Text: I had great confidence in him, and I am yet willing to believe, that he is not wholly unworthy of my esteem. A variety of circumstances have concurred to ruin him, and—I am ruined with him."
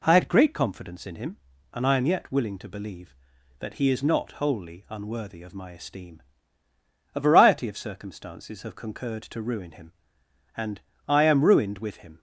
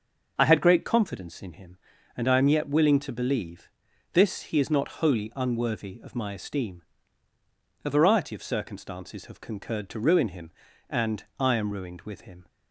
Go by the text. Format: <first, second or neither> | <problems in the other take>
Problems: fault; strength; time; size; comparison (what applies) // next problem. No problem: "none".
first | starts louder than the rest; until 1.3 s; 6.5 dB // says "this" for "that"; at 4.1 s